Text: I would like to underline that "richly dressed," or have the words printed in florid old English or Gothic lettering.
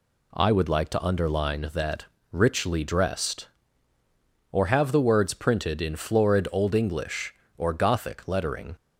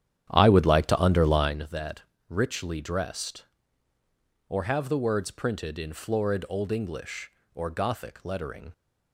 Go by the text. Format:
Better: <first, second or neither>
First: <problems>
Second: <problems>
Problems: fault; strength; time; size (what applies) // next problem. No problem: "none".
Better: first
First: pauses between "that" and "richly"; slight; at 2.0 s; 0.26 s long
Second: starts louder than the rest; strong; until 1.7 s; 10 dB // pauses between "that" and "richly"; slight; at 2.0 s; 0.26 s long